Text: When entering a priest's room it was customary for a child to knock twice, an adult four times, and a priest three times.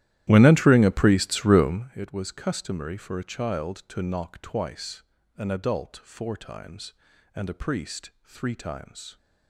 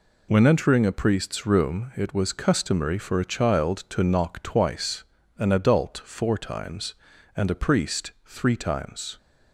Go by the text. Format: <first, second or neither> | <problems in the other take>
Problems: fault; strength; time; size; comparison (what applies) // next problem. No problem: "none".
second | starts louder than the rest; strong; until 1.9 s; 13.5 dB